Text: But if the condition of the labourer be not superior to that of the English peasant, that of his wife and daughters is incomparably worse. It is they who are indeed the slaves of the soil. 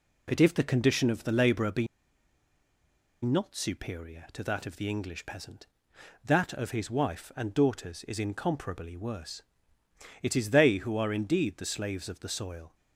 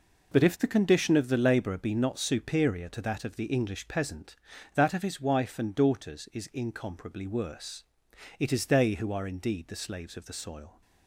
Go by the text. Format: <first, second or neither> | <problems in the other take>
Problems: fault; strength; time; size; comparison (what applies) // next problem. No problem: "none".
second | pauses between "be" and "not"; strong; at 1.8 s; 1.3 s long